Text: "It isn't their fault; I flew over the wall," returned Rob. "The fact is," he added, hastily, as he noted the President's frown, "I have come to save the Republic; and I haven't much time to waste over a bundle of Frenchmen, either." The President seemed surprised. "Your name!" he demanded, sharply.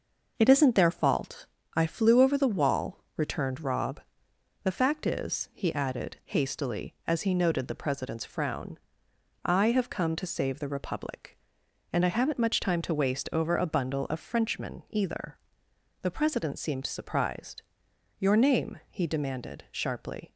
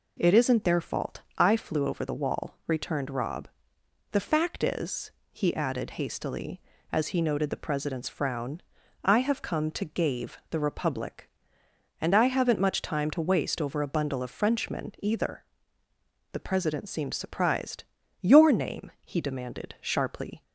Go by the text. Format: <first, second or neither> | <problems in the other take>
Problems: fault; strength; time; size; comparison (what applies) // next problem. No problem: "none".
first | says "gave" for "save"; at 9.8 s